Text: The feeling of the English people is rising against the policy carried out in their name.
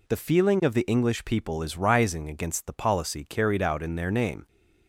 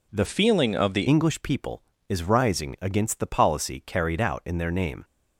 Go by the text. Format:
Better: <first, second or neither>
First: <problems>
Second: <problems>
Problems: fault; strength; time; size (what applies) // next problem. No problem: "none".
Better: first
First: none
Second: changes voice from "feeling" to "the"; from 0.2 to 1.0 s; 0.8 s long